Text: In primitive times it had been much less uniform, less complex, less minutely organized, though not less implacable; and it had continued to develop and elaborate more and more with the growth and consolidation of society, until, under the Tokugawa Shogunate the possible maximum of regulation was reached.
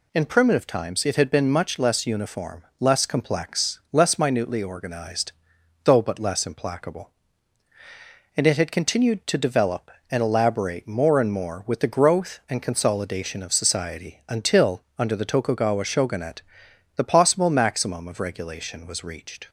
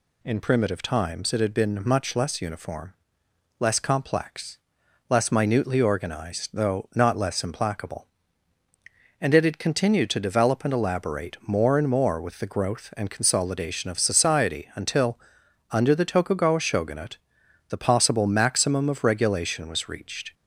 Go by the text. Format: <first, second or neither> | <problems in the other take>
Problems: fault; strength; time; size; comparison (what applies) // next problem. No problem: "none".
second | says "but" for "not"; at 6.0 s // pauses between "Shogunate" and "the"; noticeable; at 16.4 s; 0.54 s long; noticeable in the second